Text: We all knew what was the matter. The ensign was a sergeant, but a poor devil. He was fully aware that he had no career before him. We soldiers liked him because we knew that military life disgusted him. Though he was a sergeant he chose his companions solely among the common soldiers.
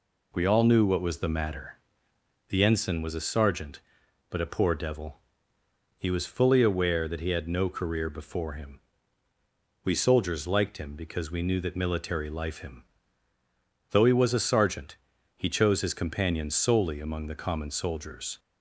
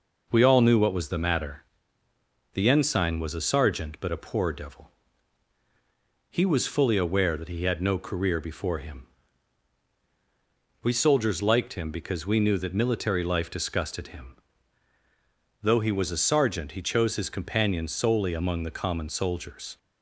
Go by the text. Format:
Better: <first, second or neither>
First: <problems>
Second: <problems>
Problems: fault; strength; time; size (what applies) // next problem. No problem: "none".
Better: second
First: skips "disgusted"; at 12.5 s // pauses between "sergeant" and "he"; at 14.9 s; 0.42 s long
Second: none